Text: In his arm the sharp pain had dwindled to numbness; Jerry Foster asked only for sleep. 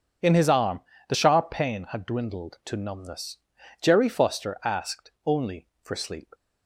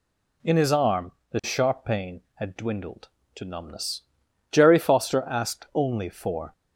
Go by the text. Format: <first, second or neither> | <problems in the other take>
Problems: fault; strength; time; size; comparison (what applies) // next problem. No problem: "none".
first | pauses between "arm" and "the"; slight; at 1.1 s; 0.20 s long; slight in the first // stops before "sleep"; at 6.5 s